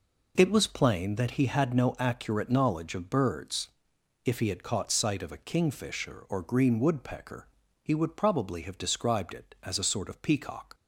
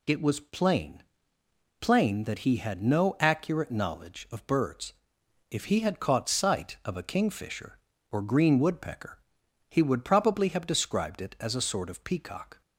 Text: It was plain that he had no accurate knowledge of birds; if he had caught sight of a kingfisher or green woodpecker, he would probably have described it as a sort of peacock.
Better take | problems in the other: first | says "plain" twice; at 1.7 s

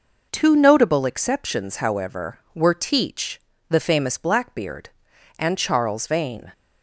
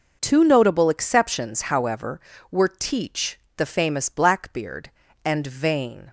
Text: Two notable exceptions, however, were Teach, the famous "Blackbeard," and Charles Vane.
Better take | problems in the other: first | skips "Charles"; at 5.4 s

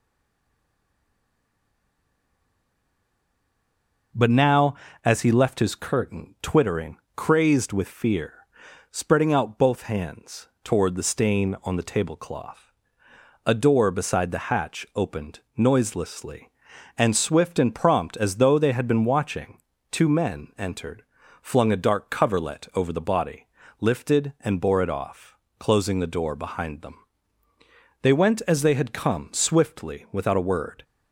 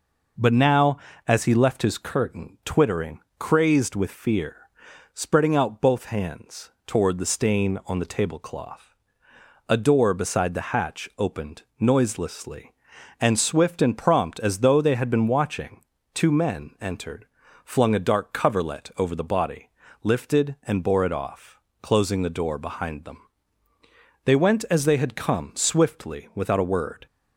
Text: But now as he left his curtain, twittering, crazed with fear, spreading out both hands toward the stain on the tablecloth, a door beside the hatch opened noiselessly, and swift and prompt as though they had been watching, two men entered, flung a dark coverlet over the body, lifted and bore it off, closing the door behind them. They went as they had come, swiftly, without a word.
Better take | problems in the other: second | stays silent before the first word; strong; until 4.1 s; 4.1 s long // pauses between "hands" and "toward"; slight; at 10.4 s; 0.16 s long; slight in the second // pauses between "opened" and "noiselessly"; slight; at 15.3 s; 0.18 s long; slight in the second

